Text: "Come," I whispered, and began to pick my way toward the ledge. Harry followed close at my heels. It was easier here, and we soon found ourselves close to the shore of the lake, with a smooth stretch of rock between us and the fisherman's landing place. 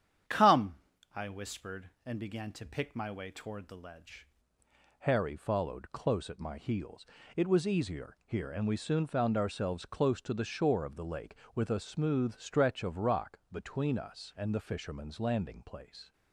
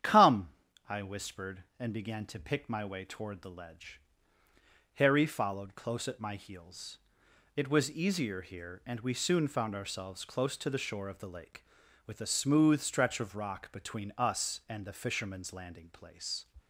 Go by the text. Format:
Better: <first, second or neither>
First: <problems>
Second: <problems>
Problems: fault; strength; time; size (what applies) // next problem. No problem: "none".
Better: second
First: starts louder than the rest; strong; until 1.6 s; 9 dB // changes voice at "Harry"; from 5.0 s on; 11.1 s long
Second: starts louder than the rest; strong; until 1.4 s; 9.5 dB